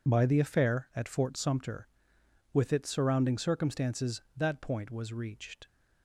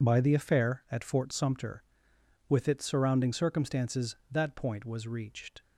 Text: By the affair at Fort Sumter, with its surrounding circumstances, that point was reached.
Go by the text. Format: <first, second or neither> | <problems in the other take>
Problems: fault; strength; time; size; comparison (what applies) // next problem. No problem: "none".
neither | none